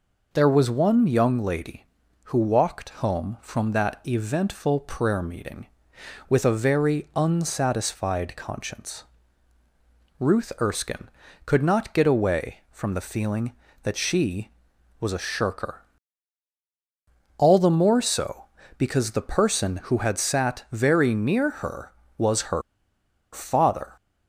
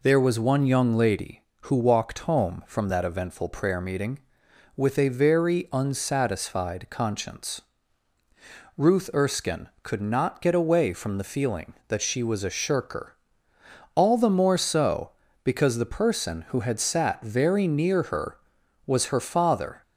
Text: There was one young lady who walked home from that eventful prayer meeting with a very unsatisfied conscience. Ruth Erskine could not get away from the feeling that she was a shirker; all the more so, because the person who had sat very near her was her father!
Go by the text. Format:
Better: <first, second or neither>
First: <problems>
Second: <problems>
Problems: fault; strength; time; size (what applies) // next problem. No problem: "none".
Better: second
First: pauses between "her" and "father"; noticeable; at 22.6 s; 0.71 s long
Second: none